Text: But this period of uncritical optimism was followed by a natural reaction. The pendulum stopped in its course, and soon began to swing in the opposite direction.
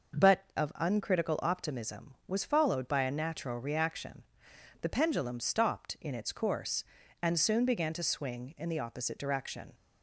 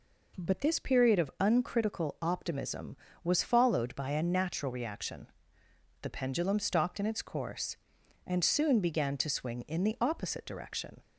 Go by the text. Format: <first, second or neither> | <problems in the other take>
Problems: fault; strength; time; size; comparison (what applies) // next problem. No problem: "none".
second | skips "this period"; at 0.5 s